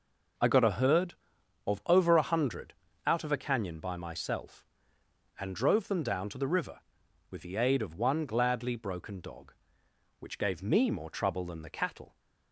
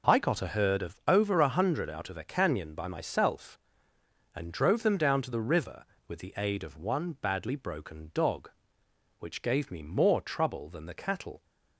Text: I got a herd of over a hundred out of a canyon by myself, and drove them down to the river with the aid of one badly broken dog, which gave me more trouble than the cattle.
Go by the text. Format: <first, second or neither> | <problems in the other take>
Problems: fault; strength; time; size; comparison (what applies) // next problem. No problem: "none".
second | pauses between "hundred" and "out"; slight; at 2.7 s; 0.32 s long // says "gladly" for "badly"; at 8.2 s